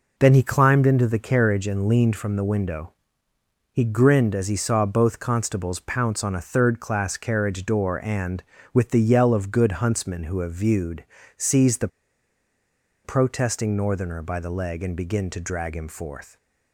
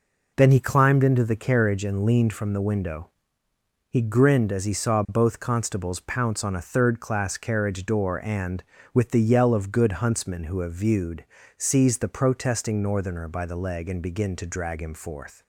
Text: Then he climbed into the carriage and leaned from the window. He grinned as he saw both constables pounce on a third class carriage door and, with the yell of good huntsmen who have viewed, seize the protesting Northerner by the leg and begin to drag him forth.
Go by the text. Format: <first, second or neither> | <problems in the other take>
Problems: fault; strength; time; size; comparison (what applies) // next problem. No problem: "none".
second | pauses between "the" and "protesting"; at 11.8 s; 1.1 s long